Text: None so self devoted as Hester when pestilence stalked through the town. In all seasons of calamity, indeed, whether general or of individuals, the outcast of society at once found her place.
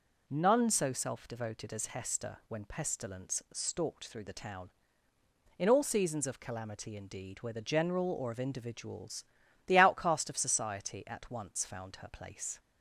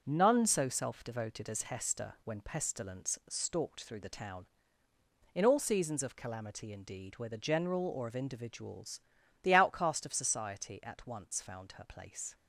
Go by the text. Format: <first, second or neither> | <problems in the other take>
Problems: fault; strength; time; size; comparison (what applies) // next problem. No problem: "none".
first | gets quieter; noticeable; throughout; 6 dB